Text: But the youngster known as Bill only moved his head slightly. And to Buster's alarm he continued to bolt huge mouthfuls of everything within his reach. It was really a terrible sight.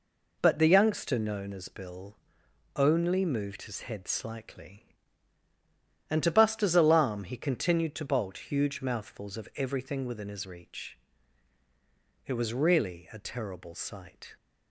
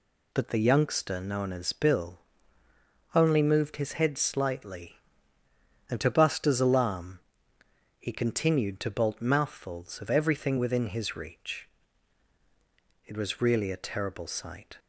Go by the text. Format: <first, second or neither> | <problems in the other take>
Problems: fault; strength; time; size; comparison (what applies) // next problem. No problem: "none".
first | pauses between "Bill" and "only"; noticeable; at 2.2 s; 0.92 s long; noticeable in the first // pauses between "alarm" and "he"; noticeable; at 7.1 s; 0.80 s long // skips "huge"; at 9.1 s